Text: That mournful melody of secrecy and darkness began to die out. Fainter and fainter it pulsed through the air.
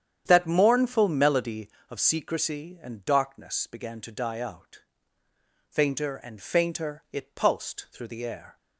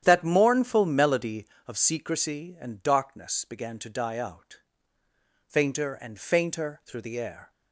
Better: first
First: starts louder than the rest; strong; until 1.2 s; 9 dB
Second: starts louder than the rest; strong; until 1.0 s; 10 dB // skips "it pulsed"; at 6.8 s

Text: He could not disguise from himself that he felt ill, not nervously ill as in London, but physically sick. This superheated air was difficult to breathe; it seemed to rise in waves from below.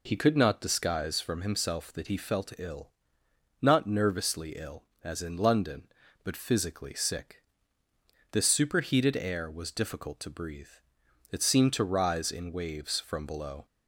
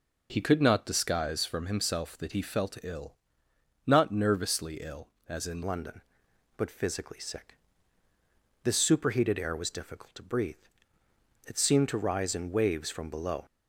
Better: first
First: none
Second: changes voice at "London"; from 5.6 s on; 7.8 s long

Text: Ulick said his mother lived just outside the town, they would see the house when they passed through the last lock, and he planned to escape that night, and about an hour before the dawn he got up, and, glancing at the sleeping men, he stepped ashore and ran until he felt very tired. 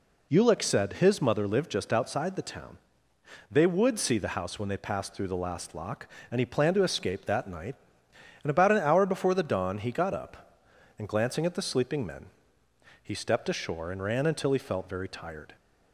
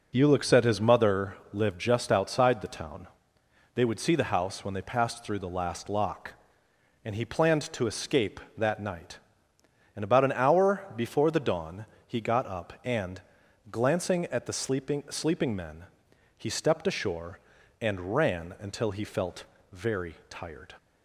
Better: first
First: none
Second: pauses between "mother" and "lived"; slight; at 1.3 s; 0.16 s long // pauses between "dawn" and "he"; slight; at 11.8 s; 0.20 s long // says "sleeping" twice; at 15.0 s // pauses between "felt" and "very"; slight; at 19.4 s; 0.26 s long // pauses between "very" and "tired"; slight; at 20.1 s; 0.16 s long

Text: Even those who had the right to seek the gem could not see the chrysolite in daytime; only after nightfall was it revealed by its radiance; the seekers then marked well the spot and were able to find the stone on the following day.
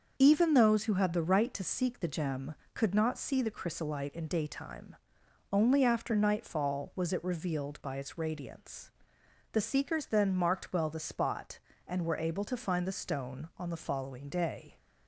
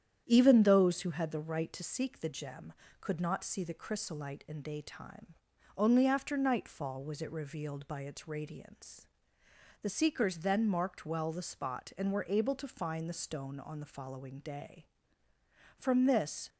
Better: first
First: starts louder than the rest; until 1.1 s; 6.5 dB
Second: starts louder than the rest; strong; until 1.2 s; 9.5 dB // goes on to say "From this"; noticeable; from 15.7 s on; 0.72 s long

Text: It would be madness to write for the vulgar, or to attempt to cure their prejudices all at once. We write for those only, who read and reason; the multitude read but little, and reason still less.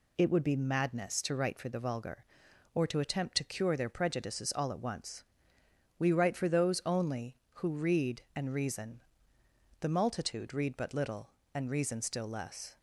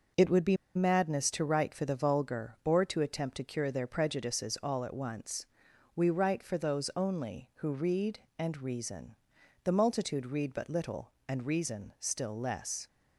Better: first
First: none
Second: pauses between "be" and "madness"; slight; at 0.5 s; 0.19 s long

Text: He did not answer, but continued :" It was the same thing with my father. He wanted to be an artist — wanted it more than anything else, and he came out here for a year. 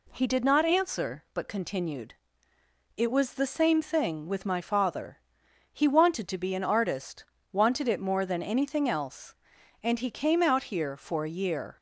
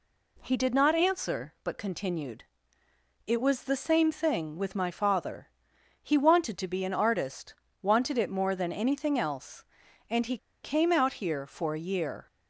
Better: first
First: none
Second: pauses between "he" and "came"; slight; at 10.3 s; 0.25 s long

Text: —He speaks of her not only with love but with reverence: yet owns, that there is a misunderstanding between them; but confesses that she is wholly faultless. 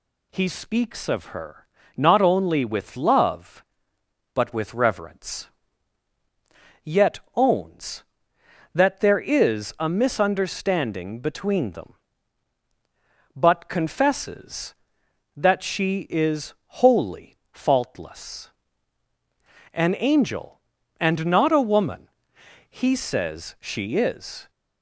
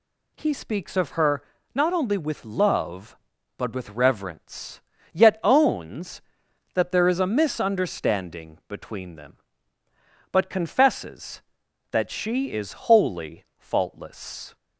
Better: second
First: pauses between "her" and "not"; slight; at 1.6 s; 0.30 s long // pauses between "is" and "wholly"; slight; at 16.5 s; 0.28 s long // pauses between "wholly" and "faultless"; slight; at 17.3 s; 0.16 s long // goes on to say "An angel and not a woman he says she is"; strong; from 19.7 s on; 4.7 s long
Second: pauses between "her" and "not"; slight; at 1.4 s; 0.30 s long

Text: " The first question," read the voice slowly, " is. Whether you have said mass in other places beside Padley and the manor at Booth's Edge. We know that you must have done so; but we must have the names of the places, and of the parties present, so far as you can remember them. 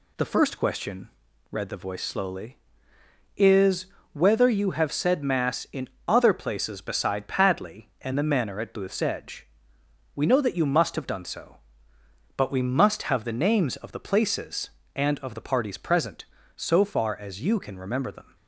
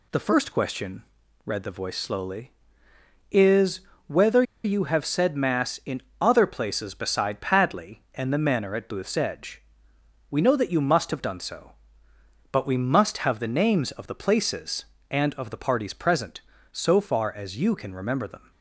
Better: first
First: pauses between "in" and "other"; slight; at 5.8 s; 0.18 s long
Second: pauses between "Whether" and "you"; slight; at 4.4 s; 0.20 s long // pauses between "in" and "other"; slight; at 6.0 s; 0.18 s long

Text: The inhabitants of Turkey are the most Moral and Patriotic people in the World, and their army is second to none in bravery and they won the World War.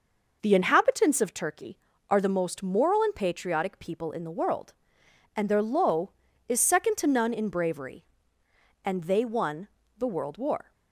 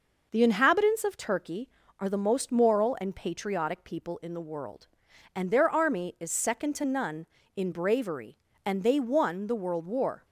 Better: second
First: says "low" for "army"; at 5.6 s // pauses between "won" and "the"; slight; at 9.6 s; 0.30 s long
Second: none

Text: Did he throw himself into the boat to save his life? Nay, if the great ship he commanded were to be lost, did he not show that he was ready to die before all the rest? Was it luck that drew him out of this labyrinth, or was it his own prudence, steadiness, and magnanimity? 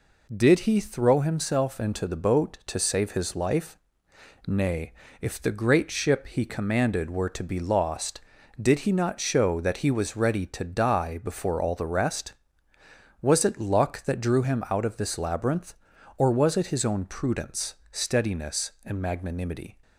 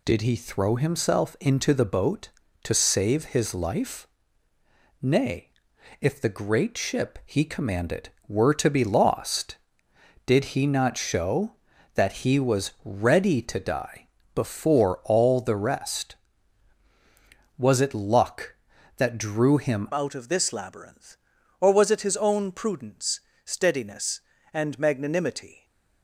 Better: first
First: none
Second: pauses between "die" and "before"; slight; at 14.0 s; 0.28 s long // changes voice at "out"; from 19.9 s on; 5.7 s long

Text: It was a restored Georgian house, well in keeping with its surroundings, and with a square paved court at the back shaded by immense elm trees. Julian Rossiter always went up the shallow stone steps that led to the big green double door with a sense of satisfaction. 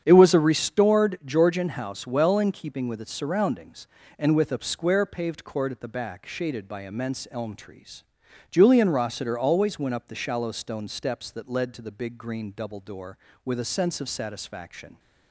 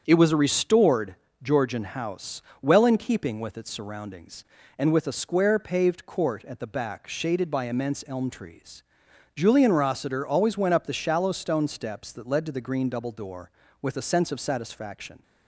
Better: first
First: starts louder than the rest; strong; until 1.0 s; 8.5 dB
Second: starts louder than the rest; strong; until 1.0 s; 7.5 dB // pauses between "restored" and "Georgian"; slight; at 1.1 s; 0.28 s long // skips "big"; at 12.6 s

